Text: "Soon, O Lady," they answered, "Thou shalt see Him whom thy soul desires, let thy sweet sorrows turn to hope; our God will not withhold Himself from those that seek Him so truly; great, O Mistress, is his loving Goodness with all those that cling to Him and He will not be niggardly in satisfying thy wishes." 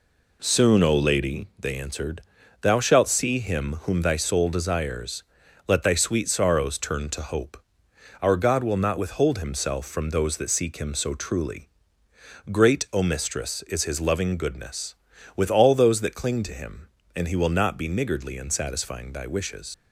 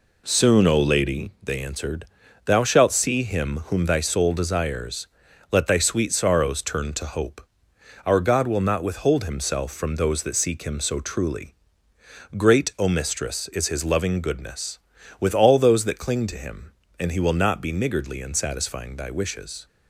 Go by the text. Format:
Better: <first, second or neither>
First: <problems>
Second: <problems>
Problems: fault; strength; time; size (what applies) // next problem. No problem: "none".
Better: second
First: leaves "wishes" unfinished; at 19.7 s; 75 ms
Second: none